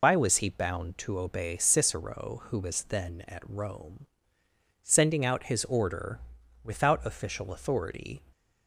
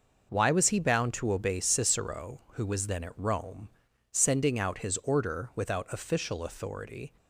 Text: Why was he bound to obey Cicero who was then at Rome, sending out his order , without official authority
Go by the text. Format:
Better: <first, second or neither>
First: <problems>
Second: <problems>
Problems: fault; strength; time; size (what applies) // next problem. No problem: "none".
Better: second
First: loses the start of "Why"; at 0.0 s; 80 ms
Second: none